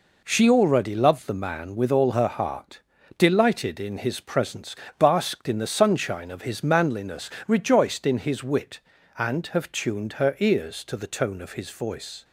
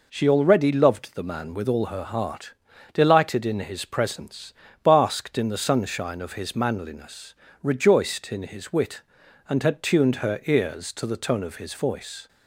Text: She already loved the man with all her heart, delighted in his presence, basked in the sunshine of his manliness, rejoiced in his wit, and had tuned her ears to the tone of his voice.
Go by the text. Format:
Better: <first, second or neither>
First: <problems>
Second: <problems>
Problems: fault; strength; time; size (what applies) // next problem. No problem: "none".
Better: second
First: says "have" for "had"; at 9.4 s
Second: none